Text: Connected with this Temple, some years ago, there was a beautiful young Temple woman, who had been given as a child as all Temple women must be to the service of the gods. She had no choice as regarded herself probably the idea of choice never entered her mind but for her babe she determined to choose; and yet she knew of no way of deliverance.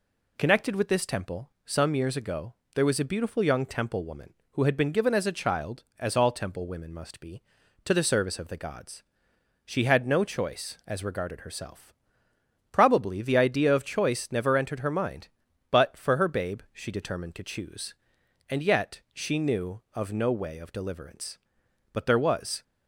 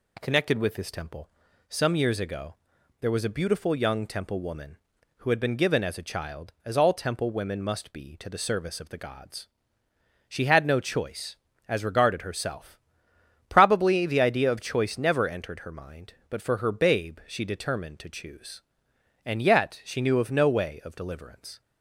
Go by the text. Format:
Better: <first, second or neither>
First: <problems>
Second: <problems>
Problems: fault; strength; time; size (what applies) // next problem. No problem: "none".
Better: second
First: pauses between "herself" and "probably"; noticeable; at 11.9 s; 0.80 s long // goes on to say "But there was"; noticeable; from 21.9 s on; 0.70 s long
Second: pauses between "herself" and "probably"; noticeable; at 12.7 s; 0.72 s long